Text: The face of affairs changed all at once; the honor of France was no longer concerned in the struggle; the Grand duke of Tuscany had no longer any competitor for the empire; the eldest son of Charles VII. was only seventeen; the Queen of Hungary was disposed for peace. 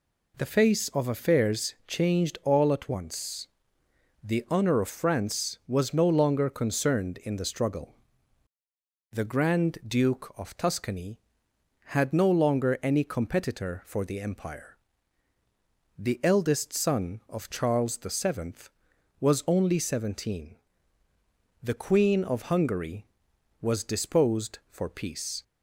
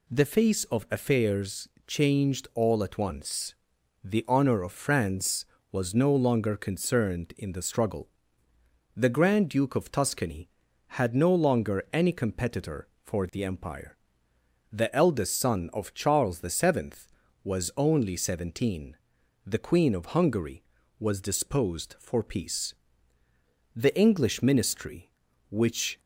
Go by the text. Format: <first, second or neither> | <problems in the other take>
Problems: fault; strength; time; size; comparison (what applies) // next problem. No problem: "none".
first | pauses between "affairs" and "changed"; slight; at 1.6 s; 0.18 s long // goes on to say "The English ministry which"; strong; from 23.7 s on; 2.2 s long